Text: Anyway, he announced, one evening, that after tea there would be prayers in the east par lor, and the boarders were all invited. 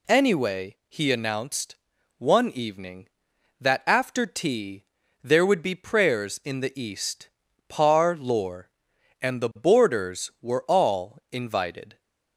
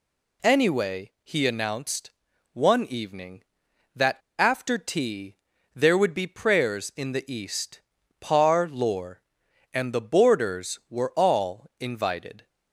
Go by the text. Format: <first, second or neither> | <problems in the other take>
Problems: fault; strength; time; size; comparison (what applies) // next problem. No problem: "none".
first | pauses between "that" and "after"; slight; at 4.1 s; 0.22 s long // pauses between "tea" and "there"; at 5.3 s; 0.40 s long; also in the first // pauses between "east" and "par"; at 7.8 s; 0.40 s long; also in the first